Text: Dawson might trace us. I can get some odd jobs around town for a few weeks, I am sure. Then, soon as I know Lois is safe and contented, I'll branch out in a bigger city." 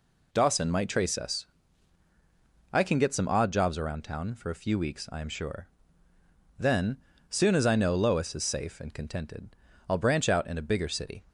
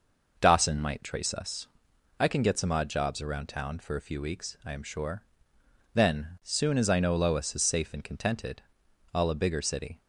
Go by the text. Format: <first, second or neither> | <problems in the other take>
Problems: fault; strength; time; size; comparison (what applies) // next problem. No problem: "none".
first | skips "branch out in"; at 9.3 s